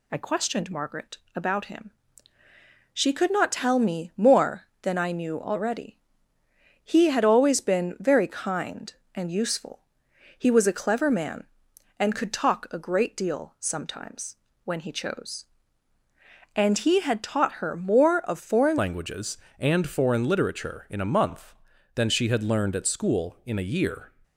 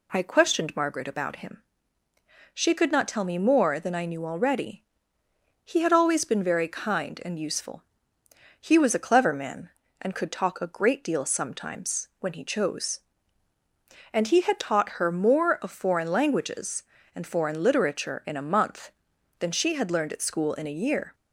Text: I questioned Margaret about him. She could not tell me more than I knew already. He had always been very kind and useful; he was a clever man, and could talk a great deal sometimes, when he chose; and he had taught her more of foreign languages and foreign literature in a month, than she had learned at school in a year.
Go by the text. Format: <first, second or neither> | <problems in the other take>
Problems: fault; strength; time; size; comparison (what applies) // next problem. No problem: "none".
second | pauses between "Margaret" and "about"; slight; at 1.1 s; 0.18 s long // changes voice at "languages"; from 18.7 s on; 5.4 s long